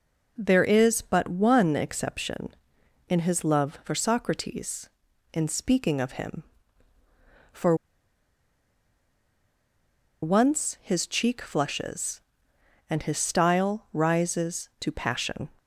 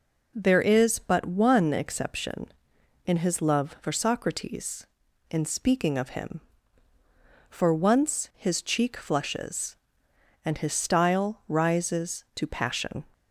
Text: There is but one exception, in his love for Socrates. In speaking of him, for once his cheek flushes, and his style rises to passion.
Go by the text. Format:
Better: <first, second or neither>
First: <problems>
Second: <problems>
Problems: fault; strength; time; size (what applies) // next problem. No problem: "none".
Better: second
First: pauses between "for" and "once"; strong; at 7.7 s; 2.4 s long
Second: none